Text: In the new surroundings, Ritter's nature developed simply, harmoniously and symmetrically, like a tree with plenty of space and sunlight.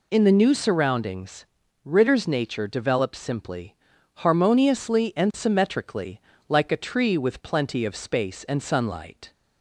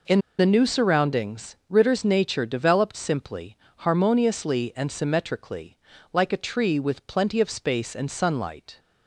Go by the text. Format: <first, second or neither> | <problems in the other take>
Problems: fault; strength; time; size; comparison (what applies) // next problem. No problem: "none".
first | pauses between "In" and "the"; slight; at 0.1 s; 0.19 s long